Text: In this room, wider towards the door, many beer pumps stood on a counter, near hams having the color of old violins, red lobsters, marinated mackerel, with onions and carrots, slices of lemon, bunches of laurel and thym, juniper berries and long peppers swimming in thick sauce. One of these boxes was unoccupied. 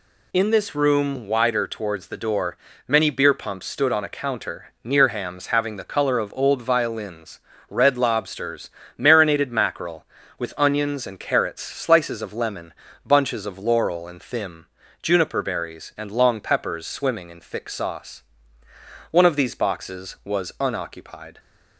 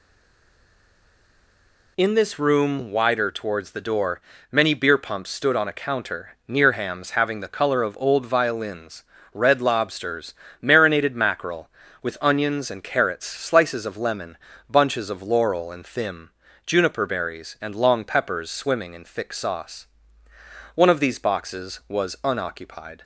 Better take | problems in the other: first | stays silent before the first word; noticeable; until 1.9 s; 1.9 s long

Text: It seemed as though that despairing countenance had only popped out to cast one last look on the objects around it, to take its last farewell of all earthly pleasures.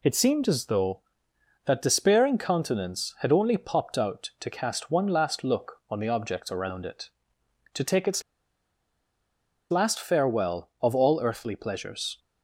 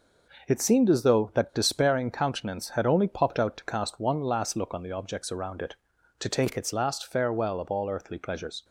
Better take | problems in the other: second | pauses between "its" and "last"; strong; at 8.2 s; 1.4 s long

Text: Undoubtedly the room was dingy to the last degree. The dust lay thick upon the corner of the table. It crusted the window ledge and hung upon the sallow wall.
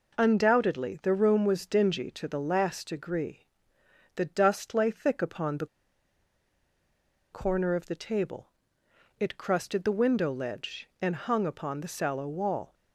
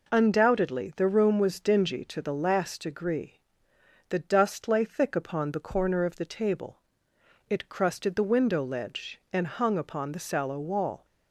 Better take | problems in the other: second | pauses between "the" and "corner"; strong; at 5.6 s; 1.6 s long

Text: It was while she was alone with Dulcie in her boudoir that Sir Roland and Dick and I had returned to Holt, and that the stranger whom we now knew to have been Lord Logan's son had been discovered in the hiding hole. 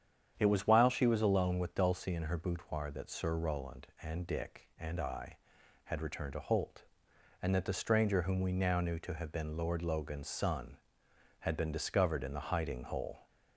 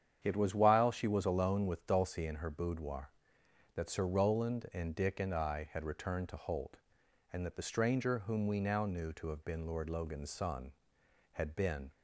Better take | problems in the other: first | starts louder than the rest; strong; until 1.2 s; 8.5 dB; strong in the first // stops before "discovered in the hiding hole"; at 11.9 s

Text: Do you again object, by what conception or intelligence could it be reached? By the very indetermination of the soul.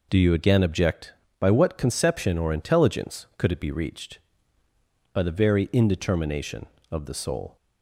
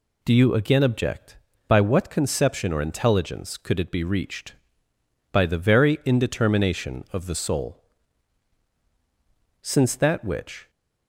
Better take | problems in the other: first | goes on to say "Since that which"; noticeable; from 9.6 s on; 1.0 s long

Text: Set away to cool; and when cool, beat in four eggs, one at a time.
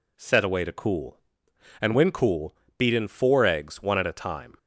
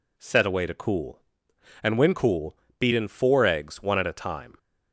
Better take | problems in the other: neither | none

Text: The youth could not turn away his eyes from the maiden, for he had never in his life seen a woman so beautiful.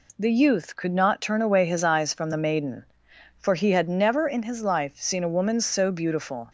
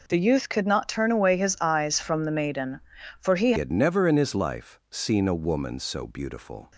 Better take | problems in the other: first | changes voice at "had"; from 3.5 s on; 3.2 s long

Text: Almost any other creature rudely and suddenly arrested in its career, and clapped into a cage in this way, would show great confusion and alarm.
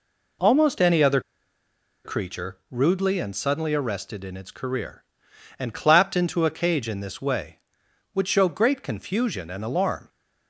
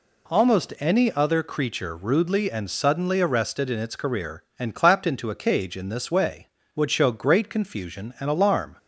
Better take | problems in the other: second | pauses between "other" and "creature"; noticeable; at 1.2 s; 0.84 s long

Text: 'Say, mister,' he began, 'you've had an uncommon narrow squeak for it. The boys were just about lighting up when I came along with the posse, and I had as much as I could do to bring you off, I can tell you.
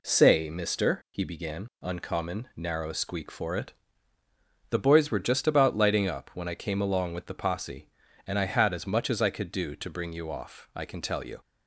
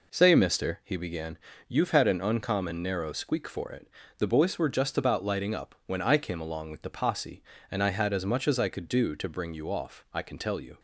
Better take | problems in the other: second | skips "you've had an"; at 1.7 s

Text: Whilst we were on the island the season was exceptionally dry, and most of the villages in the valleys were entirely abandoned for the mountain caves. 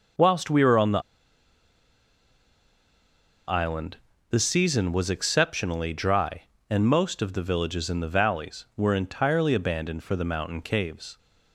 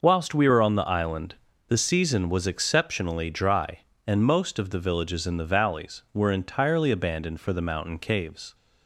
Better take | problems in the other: second | pauses between "the" and "island"; strong; at 1.0 s; 2.4 s long // pauses between "island" and "the"; slight; at 3.9 s; 0.34 s long; slight in the second

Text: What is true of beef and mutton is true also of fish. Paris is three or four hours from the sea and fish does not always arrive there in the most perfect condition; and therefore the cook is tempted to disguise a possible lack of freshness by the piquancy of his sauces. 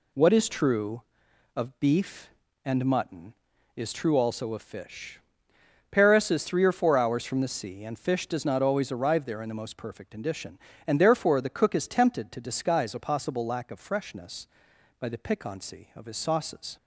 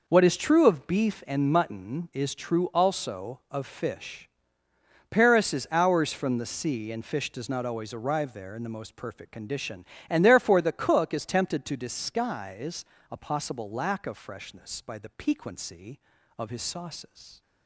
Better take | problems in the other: first | skips "three or four"; at 5.6 s // pauses between "disguise" and "a"; slight; at 12.8 s; 0.26 s long

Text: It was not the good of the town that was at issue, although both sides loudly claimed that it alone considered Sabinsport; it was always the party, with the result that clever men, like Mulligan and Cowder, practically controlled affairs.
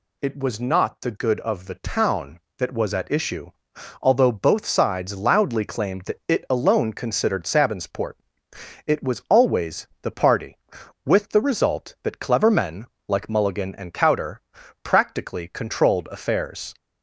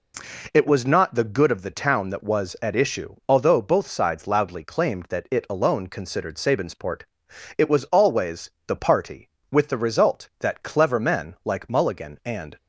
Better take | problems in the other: first | pauses between "always" and "the"; slight; at 8.4 s; 0.18 s long // stops before "Cowder practically controlled affairs"; at 12.5 s

